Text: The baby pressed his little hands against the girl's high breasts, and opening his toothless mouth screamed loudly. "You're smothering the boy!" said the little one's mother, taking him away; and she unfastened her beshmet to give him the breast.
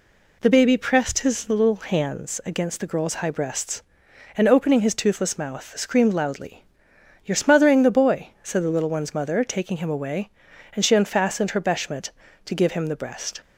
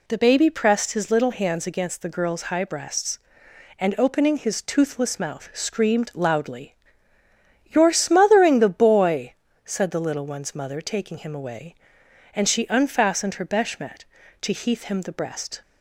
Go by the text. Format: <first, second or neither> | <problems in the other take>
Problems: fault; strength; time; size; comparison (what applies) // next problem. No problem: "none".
first | says "heath" for "give"; at 14.5 s